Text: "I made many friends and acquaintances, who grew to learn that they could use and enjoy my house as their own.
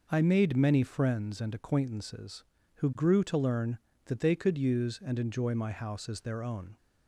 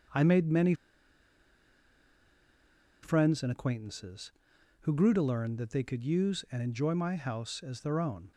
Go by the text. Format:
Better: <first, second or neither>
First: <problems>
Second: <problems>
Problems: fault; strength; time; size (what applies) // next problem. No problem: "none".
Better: first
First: none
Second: starts louder than the rest; until 3.4 s; 6.5 dB // pauses between "many" and "friends"; strong; at 0.7 s; 2.2 s long